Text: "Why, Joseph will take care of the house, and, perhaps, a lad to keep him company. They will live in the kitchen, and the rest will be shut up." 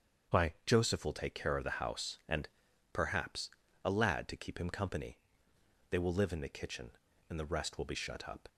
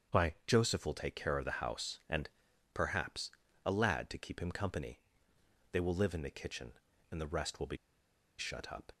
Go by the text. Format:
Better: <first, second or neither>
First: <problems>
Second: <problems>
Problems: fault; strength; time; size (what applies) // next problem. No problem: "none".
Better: first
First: starts louder than the rest; strong; until 1.4 s; 7 dB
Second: starts louder than the rest; strong; until 1.2 s; 7 dB // pauses between "be" and "shut"; noticeable; at 7.7 s; 0.62 s long